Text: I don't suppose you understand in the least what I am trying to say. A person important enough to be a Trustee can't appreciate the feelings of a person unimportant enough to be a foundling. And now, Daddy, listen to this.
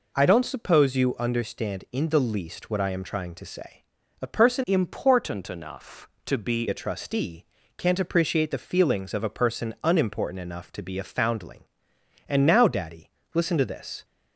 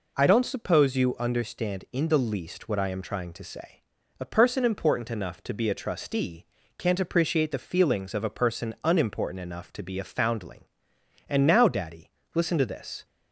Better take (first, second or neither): second